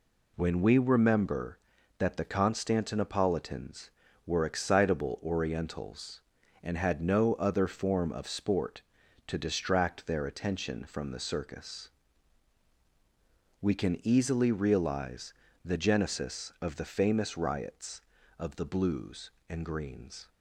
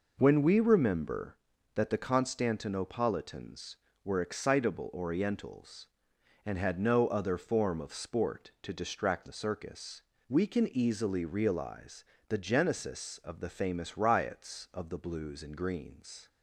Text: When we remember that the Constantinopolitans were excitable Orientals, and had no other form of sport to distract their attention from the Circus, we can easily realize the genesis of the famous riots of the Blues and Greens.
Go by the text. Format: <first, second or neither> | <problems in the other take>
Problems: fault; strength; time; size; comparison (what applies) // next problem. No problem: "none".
first | skips "their attention from"; at 9.2 s // pauses between "realize" and "the"; slight; at 12.0 s; 0.24 s long; slight in the first